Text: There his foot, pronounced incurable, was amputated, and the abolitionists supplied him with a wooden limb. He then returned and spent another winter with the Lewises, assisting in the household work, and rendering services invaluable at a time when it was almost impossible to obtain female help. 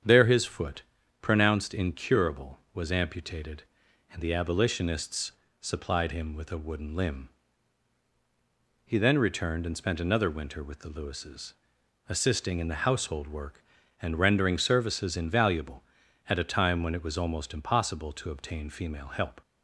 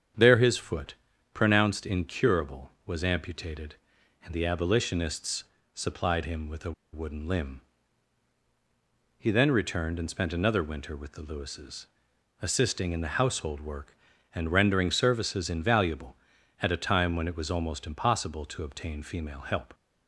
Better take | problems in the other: first | starts louder than the rest; strong; until 1.5 s; 8.5 dB; strong in the first // pauses between "abolitionists" and "supplied"; slight; at 5.4 s; 0.30 s long; slight in the first // pauses between "a" and "wooden"; slight; at 6.7 s; 0.21 s long

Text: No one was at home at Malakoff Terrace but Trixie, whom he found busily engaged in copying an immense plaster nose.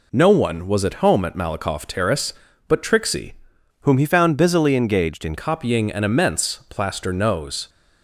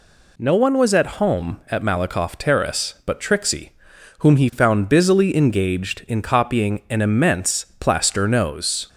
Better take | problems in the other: second | changes voice from "whom" to "in"; from 3.8 to 5.3 s; 1.5 s long

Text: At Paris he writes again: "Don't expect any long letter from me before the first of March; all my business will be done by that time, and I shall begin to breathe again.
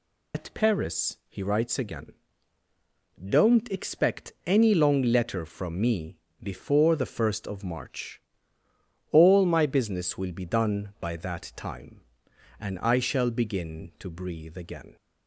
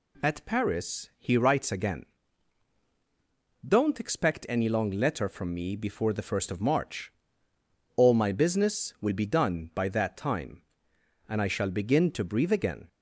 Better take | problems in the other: second | loses the start of "At"; at 0.3 s; 100 ms // pauses between "me" and "before"; slight; at 6.1 s; 0.24 s long

